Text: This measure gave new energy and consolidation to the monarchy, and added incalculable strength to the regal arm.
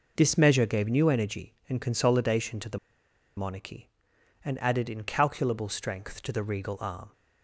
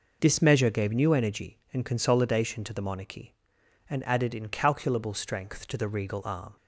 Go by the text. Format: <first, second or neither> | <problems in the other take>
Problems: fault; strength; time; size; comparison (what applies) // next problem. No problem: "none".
second | pauses between "the" and "monarchy"; noticeable; at 2.7 s; 0.59 s long